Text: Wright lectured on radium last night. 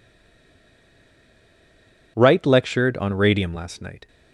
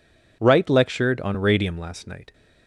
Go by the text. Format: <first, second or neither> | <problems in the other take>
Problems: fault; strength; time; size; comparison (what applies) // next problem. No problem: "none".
second | stays silent before the first word; until 2.1 s; 2.1 s long